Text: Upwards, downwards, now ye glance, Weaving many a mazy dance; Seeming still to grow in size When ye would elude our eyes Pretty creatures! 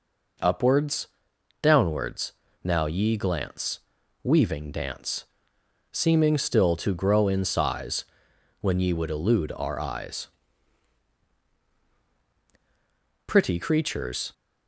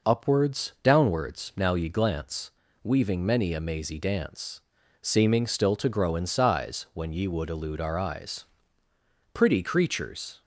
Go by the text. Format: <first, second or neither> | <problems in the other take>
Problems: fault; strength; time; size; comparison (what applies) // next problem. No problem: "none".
second | skips "many a mazy"; at 4.7 s // pauses between "size" and "When"; noticeable; at 8.0 s; 0.56 s long // pauses between "eyes" and "Pretty"; strong; at 10.2 s; 2.9 s long; noticeable in the second